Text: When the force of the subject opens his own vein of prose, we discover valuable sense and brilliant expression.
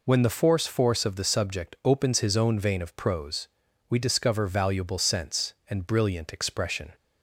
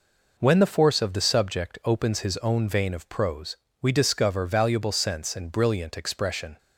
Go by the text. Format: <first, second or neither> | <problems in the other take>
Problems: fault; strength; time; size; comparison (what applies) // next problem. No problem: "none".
second | says "force" twice; at 0.6 s